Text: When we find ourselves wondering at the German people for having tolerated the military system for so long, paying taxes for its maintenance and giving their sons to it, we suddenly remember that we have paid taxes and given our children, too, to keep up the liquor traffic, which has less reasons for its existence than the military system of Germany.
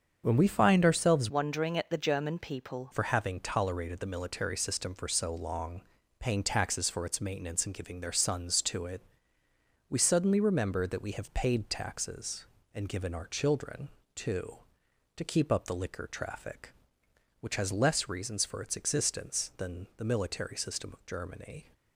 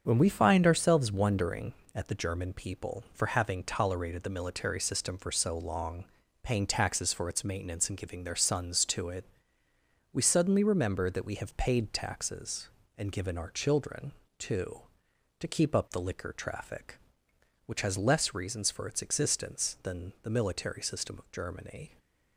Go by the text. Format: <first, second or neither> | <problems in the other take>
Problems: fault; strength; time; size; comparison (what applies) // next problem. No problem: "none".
second | starts louder than the rest; until 1.2 s; 7 dB; also in the second // changes voice from "wondering" to "people"; from 1.3 to 2.9 s; 1.6 s long